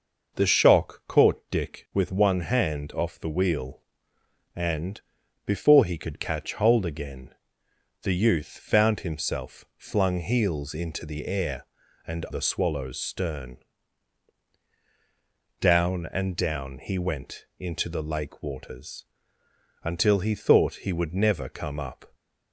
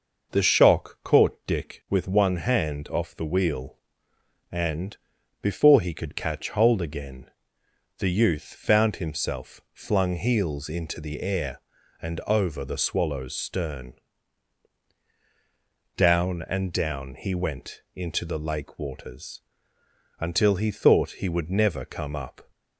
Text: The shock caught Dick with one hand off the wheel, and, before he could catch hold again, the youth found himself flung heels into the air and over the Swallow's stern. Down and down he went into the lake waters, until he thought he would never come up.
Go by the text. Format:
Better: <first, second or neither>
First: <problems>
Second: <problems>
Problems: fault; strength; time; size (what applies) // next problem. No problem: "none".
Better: second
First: skips "over"; at 12.2 s // pauses between "went" and "into"; slight; at 17.4 s; 0.16 s long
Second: pauses between "went" and "into"; slight; at 17.8 s; 0.16 s long